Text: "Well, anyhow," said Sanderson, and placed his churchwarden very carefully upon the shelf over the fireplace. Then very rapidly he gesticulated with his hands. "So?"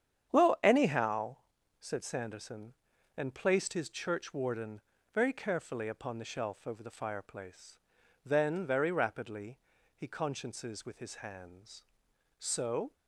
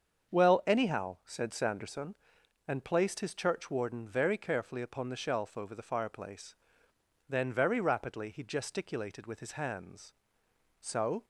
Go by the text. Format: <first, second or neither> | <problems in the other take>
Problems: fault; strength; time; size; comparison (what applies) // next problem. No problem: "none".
second | starts louder than the rest; strong; until 1.3 s; 8.5 dB; also in the second // pauses between "churchwarden" and "very"; slight; at 4.8 s; 0.34 s long // pauses between "rapidly" and "he"; at 9.5 s; 0.38 s long // says "consciences" for "gesticulated"; at 10.0 s